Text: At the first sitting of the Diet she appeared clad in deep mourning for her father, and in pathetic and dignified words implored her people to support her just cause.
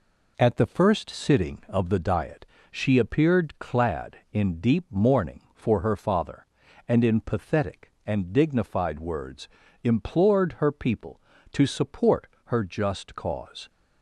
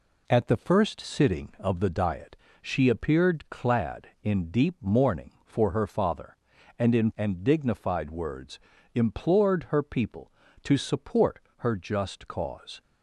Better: first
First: pauses between "Diet" and "she"; slight; at 2.4 s; 0.24 s long // pauses between "words" and "implored"; at 9.4 s; 0.38 s long // pauses between "support" and "her"; slight; at 12.2 s; 0.20 s long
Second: pauses between "Diet" and "she"; slight; at 2.3 s; 0.24 s long // skips "pathetic"; at 7.1 s // pauses between "words" and "implored"; at 8.5 s; 0.38 s long // pauses between "support" and "her"; slight; at 11.3 s; 0.20 s long

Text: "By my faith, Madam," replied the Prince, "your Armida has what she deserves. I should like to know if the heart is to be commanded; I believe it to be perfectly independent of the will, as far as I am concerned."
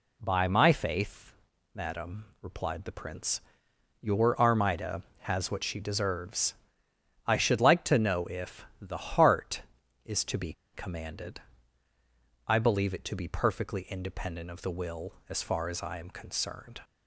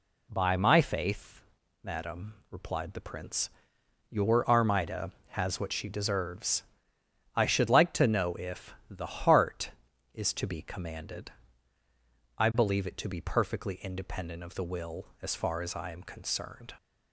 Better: second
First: pauses between "be" and "commanded"; slight; at 10.5 s; 0.20 s long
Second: none

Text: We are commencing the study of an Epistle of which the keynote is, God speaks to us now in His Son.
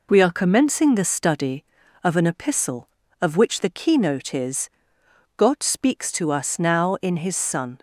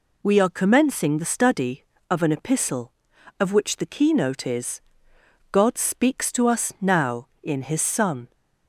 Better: neither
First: none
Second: none

